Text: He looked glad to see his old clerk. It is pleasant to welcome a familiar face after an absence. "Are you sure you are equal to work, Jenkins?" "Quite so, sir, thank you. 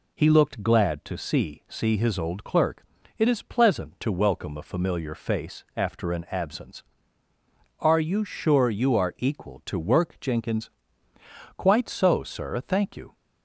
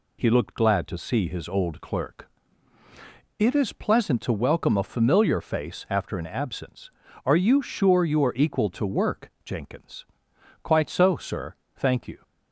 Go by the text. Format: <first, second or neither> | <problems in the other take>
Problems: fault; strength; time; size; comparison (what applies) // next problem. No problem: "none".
second | says "see" twice; at 1.6 s